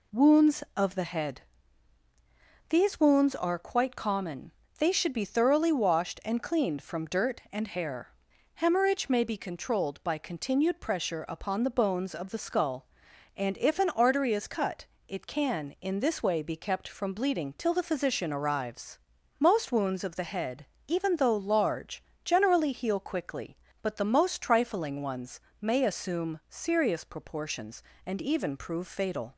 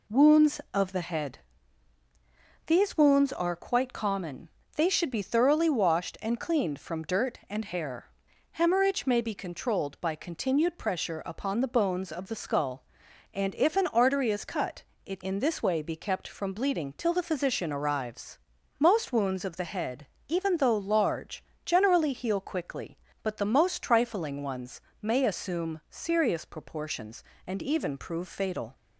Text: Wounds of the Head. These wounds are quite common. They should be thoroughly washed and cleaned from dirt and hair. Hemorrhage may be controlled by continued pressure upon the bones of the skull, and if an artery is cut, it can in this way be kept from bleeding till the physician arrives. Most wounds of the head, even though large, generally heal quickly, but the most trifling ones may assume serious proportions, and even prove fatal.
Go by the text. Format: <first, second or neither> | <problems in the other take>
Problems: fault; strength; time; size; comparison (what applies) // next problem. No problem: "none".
first | skips "can"; at 15.2 s // pauses between "ones" and "may"; slight; at 24.7 s; 0.22 s long; slight in the first